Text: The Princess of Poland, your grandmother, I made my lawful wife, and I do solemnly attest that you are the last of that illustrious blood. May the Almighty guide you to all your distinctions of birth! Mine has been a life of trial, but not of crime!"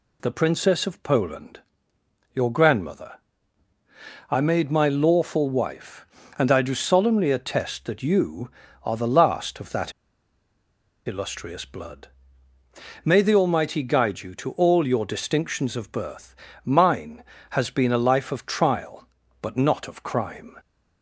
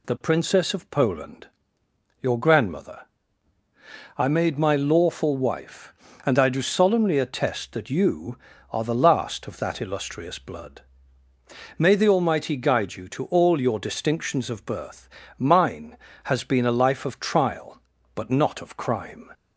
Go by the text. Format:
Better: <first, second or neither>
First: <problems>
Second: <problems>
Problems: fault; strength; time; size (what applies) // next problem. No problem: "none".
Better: second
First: pauses between "that" and "illustrious"; at 9.9 s; 1.1 s long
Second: none